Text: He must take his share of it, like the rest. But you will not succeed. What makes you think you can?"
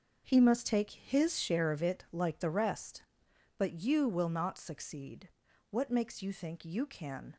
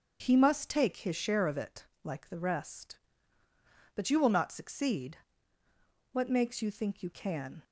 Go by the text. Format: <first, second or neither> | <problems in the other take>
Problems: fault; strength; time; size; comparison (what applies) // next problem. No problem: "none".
second | gets quieter; strong; throughout; 10.5 dB